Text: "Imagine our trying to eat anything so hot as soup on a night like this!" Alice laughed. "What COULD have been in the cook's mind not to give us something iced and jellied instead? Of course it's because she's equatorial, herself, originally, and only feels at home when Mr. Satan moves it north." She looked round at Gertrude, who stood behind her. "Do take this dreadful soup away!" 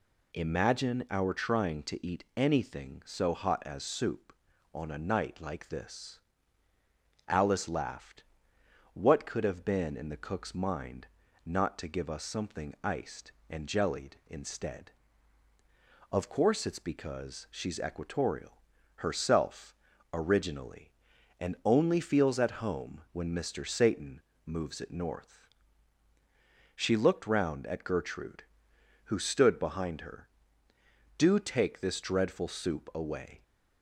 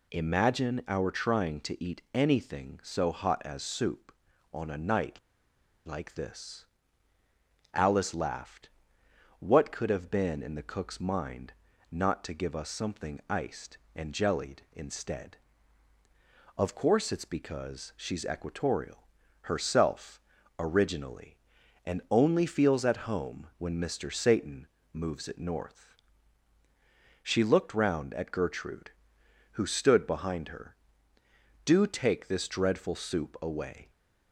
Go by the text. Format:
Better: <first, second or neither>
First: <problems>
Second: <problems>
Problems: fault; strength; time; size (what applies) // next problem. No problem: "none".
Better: first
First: pauses between "mind" and "not"; at 11.0 s; 0.40 s long // pauses between "Satan" and "moves"; slight; at 24.1 s; 0.24 s long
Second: pauses between "night" and "like"; noticeable; at 5.1 s; 0.66 s long // pauses between "mind" and "not"; at 11.5 s; 0.40 s long // pauses between "Satan" and "moves"; slight; at 24.6 s; 0.26 s long